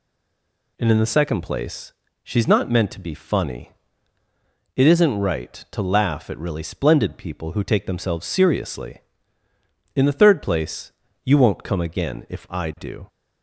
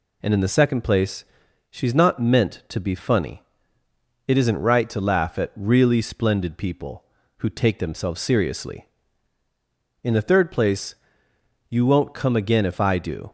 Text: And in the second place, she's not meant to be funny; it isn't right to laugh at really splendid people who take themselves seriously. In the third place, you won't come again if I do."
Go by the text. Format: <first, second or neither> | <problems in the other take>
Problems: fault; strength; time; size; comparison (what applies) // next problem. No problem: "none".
second | stays silent before the first word; slight; until 0.7 s; 0.7 s long